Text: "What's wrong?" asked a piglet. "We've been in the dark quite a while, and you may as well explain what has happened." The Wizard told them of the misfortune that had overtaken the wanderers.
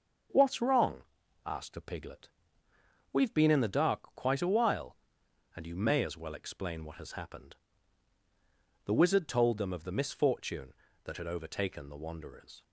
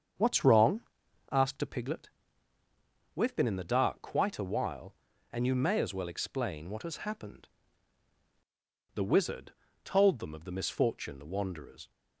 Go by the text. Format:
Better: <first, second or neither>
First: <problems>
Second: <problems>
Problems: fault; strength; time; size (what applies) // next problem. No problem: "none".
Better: first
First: starts louder than the rest; until 1.7 s; 6.5 dB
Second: starts louder than the rest; strong; until 1.6 s; 7.5 dB // pauses between "Wizard" and "told"; slight; at 9.5 s; 0.32 s long // skips "that had overtaken"; at 11.1 s